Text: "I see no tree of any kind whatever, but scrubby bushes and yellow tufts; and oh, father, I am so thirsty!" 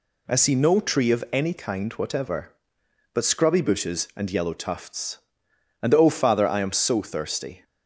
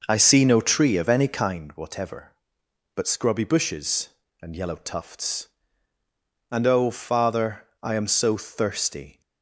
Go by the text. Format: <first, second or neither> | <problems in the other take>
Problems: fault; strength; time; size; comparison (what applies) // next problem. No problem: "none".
first | starts louder than the rest; noticeable; until 1.6 s; 5.5 dB